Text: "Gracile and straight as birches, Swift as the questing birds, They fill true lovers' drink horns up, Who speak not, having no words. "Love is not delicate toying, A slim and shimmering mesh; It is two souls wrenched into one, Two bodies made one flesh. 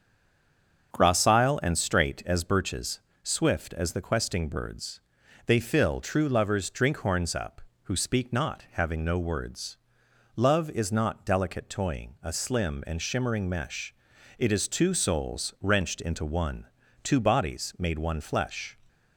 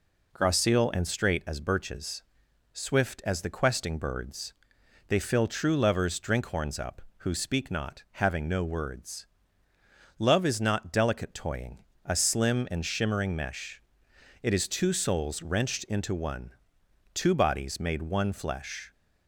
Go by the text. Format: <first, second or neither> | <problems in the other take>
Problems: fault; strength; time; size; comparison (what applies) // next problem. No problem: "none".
second | stays silent before the first word; slight; until 0.9 s; 0.9 s long // starts louder than the rest; until 1.9 s; 6.5 dB